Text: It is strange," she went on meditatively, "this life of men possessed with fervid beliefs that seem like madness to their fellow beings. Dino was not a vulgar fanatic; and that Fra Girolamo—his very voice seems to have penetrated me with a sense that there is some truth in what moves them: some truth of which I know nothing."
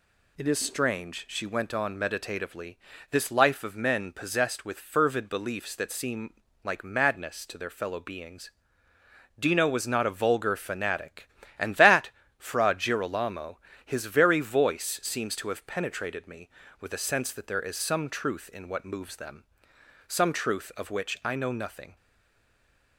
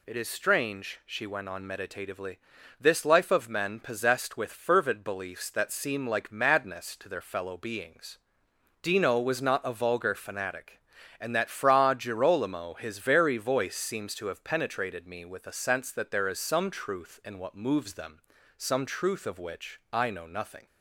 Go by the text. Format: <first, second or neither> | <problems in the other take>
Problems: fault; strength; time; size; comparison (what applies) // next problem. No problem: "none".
second | pauses between "seem" and "like"; slight; at 6.3 s; 0.30 s long // pauses between "that" and "Fra"; slight; at 12.1 s; 0.26 s long // stays silent after the last word; from 21.9 s on; 1.0 s long